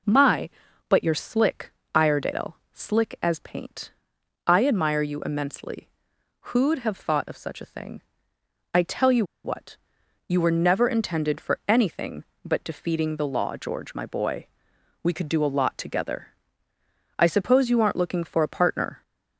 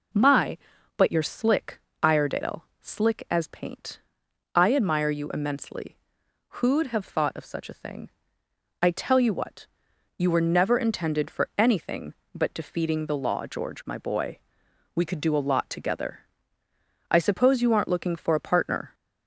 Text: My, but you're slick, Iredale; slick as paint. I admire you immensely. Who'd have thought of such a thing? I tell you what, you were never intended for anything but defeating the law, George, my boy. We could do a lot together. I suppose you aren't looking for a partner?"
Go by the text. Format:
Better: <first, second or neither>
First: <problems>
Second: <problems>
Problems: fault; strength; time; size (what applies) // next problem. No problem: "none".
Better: second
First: pauses between "you" and "what"; slight; at 9.2 s; 0.20 s long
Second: none